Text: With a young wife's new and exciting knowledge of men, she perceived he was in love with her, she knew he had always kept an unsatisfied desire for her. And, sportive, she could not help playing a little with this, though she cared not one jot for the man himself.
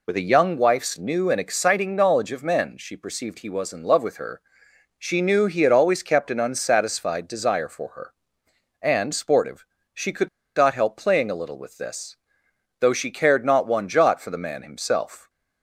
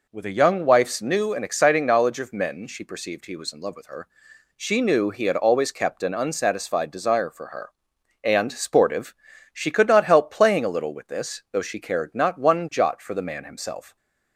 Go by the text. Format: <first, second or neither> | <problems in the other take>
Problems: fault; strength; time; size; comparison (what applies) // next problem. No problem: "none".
second | pauses between "could" and "not"; slight; at 10.2 s; 0.29 s long